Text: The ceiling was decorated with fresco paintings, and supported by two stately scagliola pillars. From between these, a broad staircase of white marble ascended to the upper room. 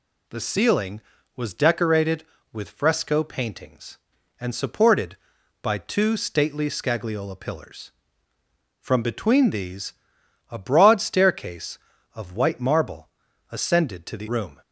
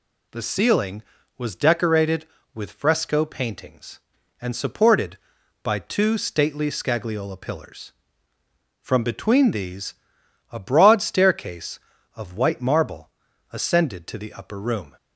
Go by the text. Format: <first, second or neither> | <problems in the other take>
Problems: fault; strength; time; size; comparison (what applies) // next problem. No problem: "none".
second | pauses between "marble" and "ascended"; at 13.0 s; 0.42 s long; also in the second // skips "upper"; at 14.2 s